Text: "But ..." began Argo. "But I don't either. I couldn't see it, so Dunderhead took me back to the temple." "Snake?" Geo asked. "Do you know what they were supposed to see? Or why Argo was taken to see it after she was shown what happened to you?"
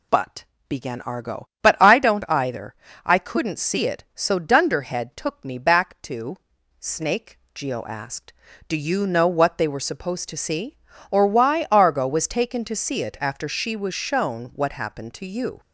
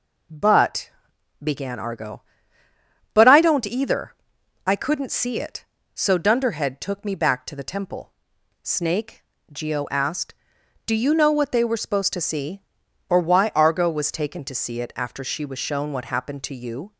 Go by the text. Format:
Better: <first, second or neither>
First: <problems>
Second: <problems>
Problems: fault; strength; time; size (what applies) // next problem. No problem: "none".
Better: second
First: skips "the temple"; at 6.5 s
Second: none